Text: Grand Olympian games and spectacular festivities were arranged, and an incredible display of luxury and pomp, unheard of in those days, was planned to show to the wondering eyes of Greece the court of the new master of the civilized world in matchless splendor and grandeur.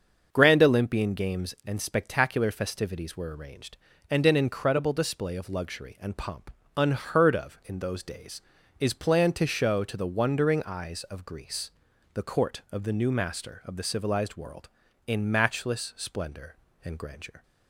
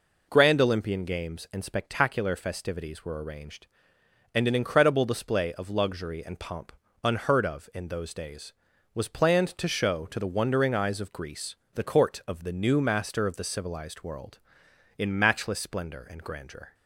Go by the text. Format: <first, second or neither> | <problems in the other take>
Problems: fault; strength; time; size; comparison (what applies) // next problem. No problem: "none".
second | starts louder than the rest; until 1.3 s; 6.5 dB // says "is" for "was"; at 8.7 s // pauses between "Greece" and "the"; at 11.7 s; 0.42 s long; slight in the second